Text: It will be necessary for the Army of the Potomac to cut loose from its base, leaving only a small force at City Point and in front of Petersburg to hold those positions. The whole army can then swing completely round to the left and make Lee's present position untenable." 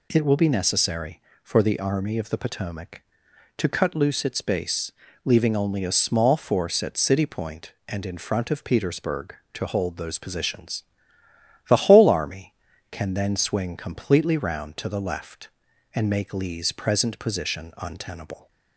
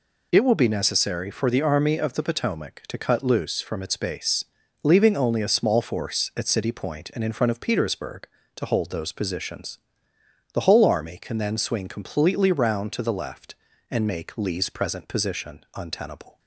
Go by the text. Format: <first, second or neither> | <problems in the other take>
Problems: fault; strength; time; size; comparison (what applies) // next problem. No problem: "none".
second | skips "from"; at 4.2 s